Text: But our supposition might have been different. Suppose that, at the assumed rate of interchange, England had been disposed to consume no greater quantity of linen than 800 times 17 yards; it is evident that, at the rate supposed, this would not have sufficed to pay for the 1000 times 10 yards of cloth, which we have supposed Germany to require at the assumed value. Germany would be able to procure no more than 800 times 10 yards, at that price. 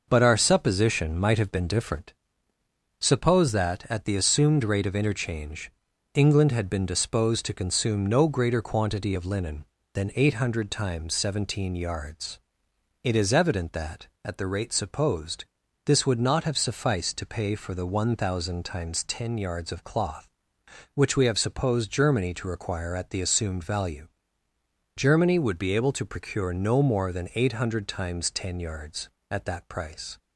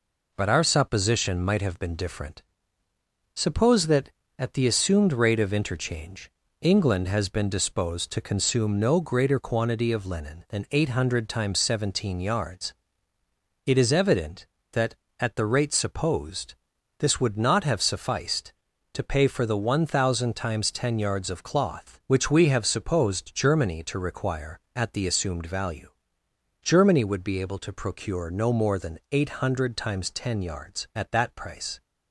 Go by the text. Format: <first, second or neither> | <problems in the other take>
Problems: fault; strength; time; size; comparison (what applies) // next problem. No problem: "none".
first | says "has" for "had"; at 7.0 s